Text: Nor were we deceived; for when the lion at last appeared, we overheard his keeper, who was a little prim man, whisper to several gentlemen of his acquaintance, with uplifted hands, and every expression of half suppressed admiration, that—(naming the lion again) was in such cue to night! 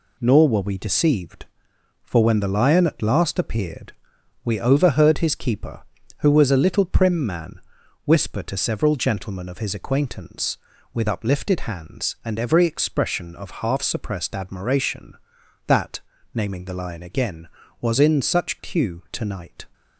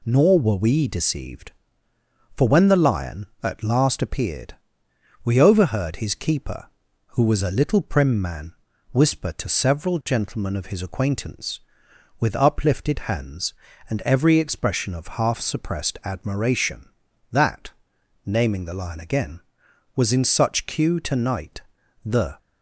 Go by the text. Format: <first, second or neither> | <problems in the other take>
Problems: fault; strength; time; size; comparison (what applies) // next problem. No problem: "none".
first | goes on to say "The"; slight; from 22.0 s on; 0.32 s long